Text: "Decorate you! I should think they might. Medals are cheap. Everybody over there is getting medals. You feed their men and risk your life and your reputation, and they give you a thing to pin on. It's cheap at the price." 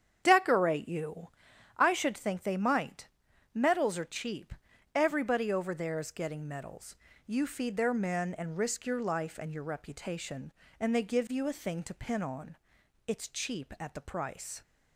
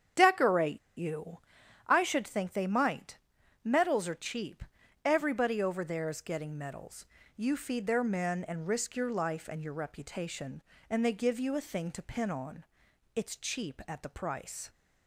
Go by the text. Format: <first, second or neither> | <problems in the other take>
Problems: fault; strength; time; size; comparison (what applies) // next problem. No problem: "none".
first | starts louder than the rest; strong; until 1.3 s; 8 dB; strong in the first // pauses between "Decorate" and "you"; slight; at 0.7 s; 0.19 s long